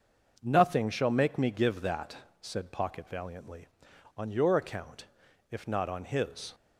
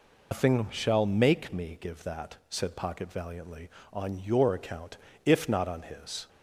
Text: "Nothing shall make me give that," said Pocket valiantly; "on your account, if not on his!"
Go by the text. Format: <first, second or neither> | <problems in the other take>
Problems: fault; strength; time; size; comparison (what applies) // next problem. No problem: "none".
first | loses the start of "Nothing"; at 0.3 s; 135 ms